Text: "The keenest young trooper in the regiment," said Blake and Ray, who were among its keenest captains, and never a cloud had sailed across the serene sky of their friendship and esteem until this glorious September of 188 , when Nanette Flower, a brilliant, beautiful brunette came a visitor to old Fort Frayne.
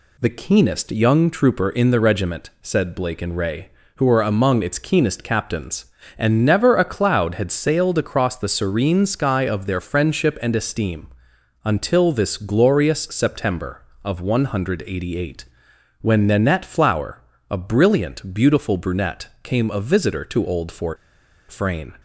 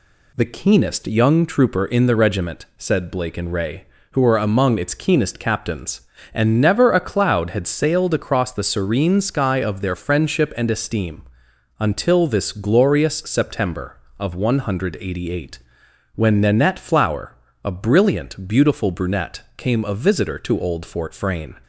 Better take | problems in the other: second | pauses between "esteem" and "until"; noticeable; at 11.0 s; 0.56 s long; noticeable in the second // pauses between "brunette" and "came"; slight; at 19.2 s; 0.16 s long; slight in the second // pauses between "Fort" and "Frayne"; noticeable; at 20.9 s; 0.54 s long

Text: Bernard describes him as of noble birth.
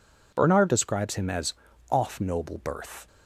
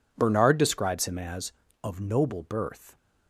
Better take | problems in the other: second | says "off" for "of"; at 1.9 s

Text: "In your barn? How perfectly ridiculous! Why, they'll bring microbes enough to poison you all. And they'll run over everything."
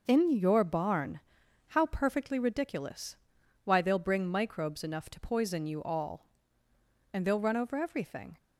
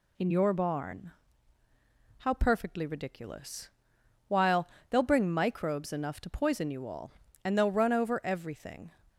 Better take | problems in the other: first | says "While" for "Why"; at 4.2 s

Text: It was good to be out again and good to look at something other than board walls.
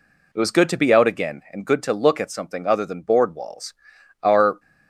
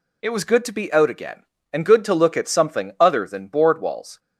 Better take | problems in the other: second | goes on to say "Our"; slight; from 4.2 s on; 0.36 s long

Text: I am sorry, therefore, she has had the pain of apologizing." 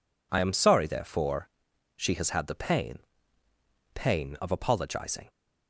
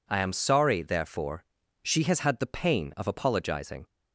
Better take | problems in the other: second | says "pain" twice; at 3.9 s

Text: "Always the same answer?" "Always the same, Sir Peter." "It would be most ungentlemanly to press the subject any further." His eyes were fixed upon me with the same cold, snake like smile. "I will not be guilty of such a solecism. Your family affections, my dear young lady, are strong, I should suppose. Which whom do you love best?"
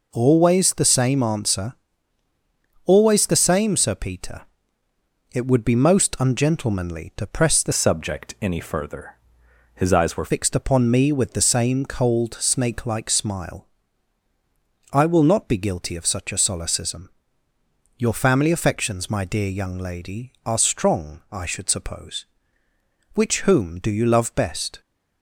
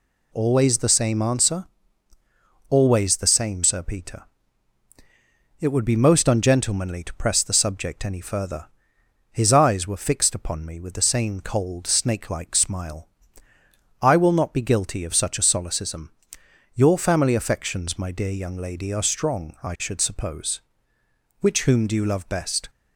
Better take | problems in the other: second | changes voice from "subject" to "were"; from 7.7 to 10.3 s; 2.6 s long

